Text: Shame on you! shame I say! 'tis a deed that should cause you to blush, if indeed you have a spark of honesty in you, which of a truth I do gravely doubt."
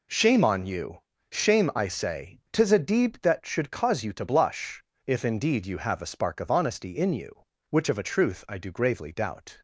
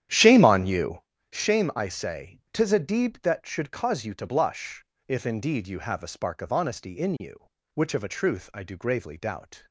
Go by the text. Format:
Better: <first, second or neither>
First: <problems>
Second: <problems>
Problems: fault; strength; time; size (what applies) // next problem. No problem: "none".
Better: first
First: none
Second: starts louder than the rest; strong; until 1.1 s; 10.5 dB